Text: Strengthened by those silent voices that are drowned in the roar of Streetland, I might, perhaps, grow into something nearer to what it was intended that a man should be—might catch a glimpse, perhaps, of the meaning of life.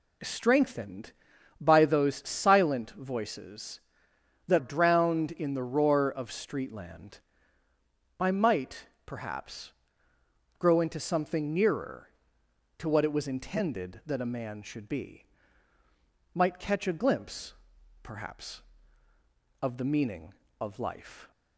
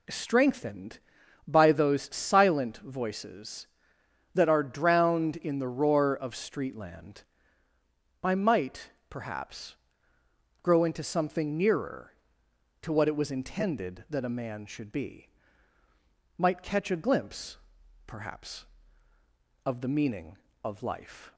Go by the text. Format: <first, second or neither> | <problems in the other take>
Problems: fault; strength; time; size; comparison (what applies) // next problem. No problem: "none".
second | skips "are"; at 4.5 s